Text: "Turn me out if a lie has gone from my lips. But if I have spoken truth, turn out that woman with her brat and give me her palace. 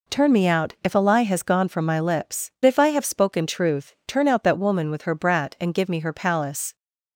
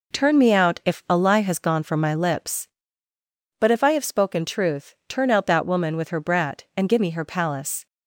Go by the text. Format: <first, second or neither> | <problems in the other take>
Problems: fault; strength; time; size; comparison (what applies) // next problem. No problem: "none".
second | skips "But"; at 2.5 s